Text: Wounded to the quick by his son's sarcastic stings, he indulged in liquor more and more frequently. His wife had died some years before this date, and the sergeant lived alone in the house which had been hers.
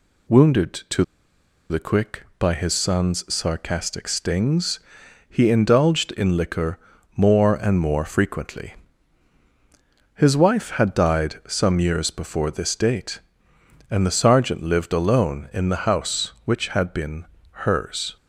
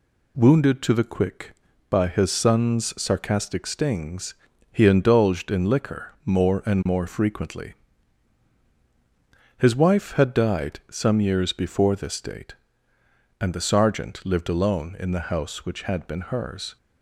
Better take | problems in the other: second | pauses between "to" and "the"; noticeable; at 1.0 s; 0.65 s long // pauses between "liquor" and "more"; at 6.7 s; 0.38 s long // pauses between "been" and "hers"; slight; at 17.2 s; 0.28 s long

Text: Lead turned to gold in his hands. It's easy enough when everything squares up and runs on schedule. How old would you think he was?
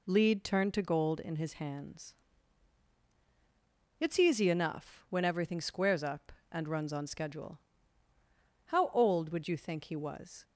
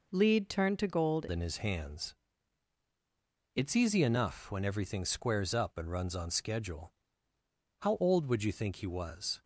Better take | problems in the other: first | changes voice at "in"; from 1.3 s on; 8.1 s long

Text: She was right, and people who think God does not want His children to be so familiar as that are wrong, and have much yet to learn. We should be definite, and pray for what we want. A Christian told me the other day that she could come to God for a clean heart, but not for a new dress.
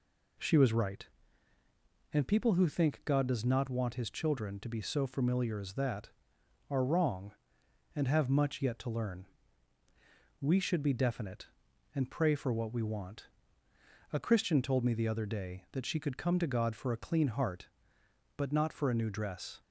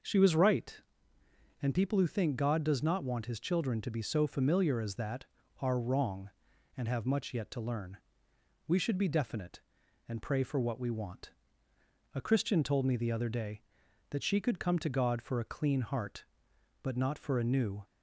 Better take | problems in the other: first | stops before "dress"; at 17.8 s

